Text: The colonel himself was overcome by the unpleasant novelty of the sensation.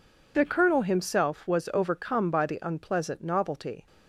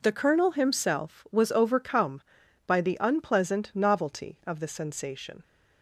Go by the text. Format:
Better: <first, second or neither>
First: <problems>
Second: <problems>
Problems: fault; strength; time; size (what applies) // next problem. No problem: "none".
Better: second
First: stops before "of the sensation"; at 3.8 s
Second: none